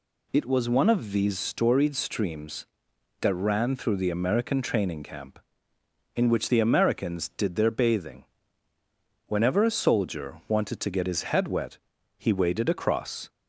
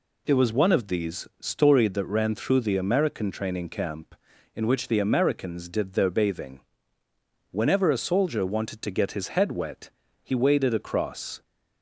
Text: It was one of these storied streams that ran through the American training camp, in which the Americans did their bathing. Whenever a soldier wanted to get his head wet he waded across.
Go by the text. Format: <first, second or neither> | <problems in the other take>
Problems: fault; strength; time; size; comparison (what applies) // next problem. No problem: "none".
first | skips "streams"; at 1.9 s // pauses between "wet" and "he"; slight; at 9.9 s; 0.32 s long; also in the first